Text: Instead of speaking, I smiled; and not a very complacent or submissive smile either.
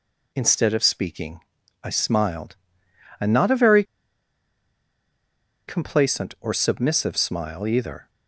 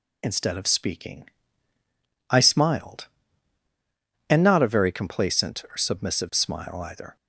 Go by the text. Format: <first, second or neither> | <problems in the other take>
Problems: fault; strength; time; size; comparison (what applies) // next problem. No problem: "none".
second | pauses between "very" and "complacent"; strong; at 3.8 s; 1.8 s long